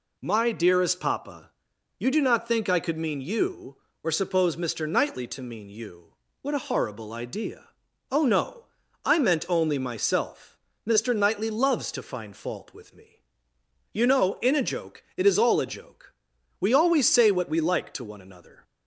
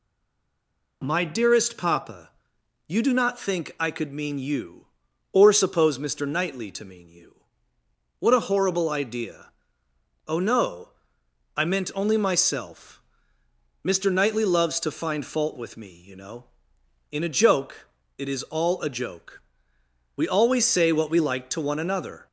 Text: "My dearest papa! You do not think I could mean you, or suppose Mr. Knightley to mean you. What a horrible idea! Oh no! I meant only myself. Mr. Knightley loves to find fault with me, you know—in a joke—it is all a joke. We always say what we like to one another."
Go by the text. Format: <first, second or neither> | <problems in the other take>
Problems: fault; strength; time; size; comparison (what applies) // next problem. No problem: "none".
first | stays silent before the first word; until 1.0 s; 1.0 s long